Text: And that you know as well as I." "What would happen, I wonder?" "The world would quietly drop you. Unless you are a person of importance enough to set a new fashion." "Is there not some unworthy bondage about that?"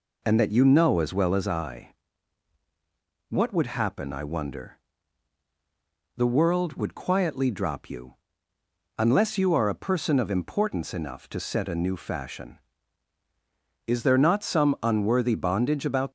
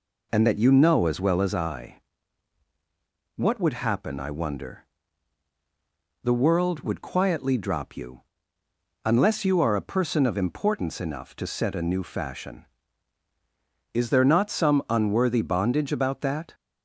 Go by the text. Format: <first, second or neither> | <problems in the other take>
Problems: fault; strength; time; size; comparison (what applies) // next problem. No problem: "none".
second | stops before "that"; at 16.0 s